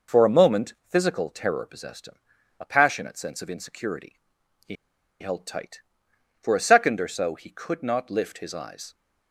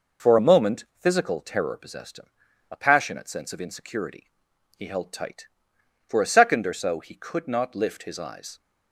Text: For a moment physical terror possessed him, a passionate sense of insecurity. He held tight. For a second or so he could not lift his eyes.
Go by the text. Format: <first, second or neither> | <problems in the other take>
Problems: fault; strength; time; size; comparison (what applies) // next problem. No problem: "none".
second | pauses between "He" and "held"; noticeable; at 4.7 s; 0.47 s long